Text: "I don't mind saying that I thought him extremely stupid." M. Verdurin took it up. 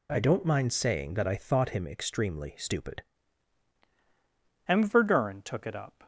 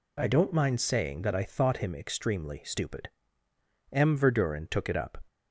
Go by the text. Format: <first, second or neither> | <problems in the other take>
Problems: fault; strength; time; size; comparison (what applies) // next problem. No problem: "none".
second | changes voice at "M"; from 4.6 s on; 1.4 s long